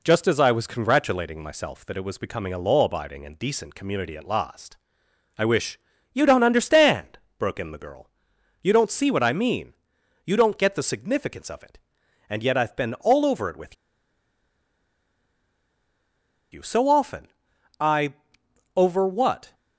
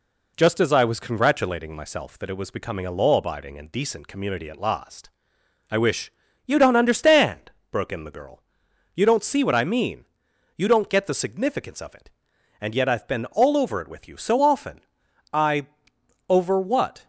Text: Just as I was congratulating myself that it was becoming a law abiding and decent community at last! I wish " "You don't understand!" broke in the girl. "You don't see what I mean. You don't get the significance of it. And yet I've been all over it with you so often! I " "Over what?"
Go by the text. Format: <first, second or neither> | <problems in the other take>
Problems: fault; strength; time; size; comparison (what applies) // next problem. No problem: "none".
second | pauses between "with" and "you"; strong; at 13.7 s; 2.7 s long